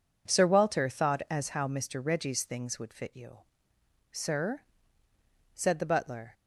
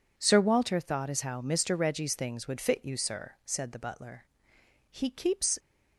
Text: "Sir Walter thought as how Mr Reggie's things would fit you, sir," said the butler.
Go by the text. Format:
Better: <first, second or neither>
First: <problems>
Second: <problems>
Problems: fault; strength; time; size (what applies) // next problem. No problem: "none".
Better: first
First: none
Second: goes on to say "He keeps"; noticeable; from 4.8 s on; 0.70 s long